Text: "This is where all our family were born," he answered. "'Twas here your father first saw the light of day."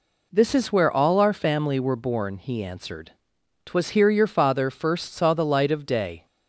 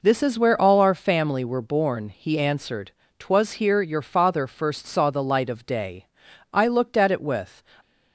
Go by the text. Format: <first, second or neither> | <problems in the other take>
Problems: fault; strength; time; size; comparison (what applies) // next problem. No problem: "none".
first | goes on to say "I looked at it with"; noticeable; from 6.5 s on; 1.0 s long